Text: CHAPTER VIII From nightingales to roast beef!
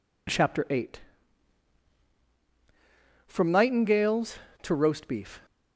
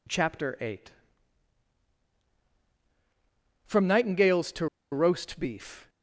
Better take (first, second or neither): first